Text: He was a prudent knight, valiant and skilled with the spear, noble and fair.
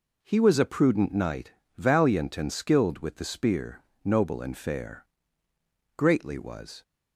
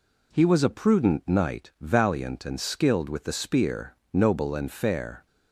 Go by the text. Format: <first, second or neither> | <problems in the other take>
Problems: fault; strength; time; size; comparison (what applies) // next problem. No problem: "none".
second | goes on to say "Greatly was"; noticeable; from 5.9 s on; 0.86 s long